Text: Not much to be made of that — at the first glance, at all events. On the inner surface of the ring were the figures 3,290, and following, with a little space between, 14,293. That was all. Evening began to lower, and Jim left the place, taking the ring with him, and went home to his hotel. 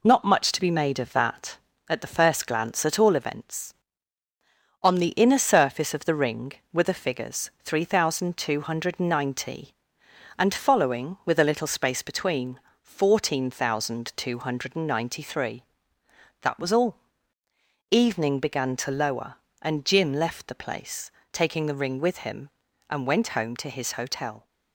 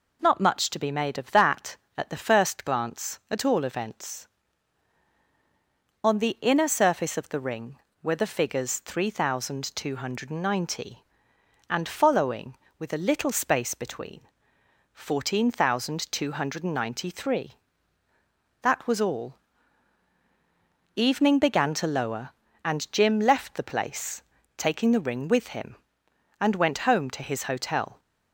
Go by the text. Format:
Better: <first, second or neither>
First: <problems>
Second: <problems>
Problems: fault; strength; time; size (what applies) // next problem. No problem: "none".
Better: second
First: gets quieter; throughout; 4 dB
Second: none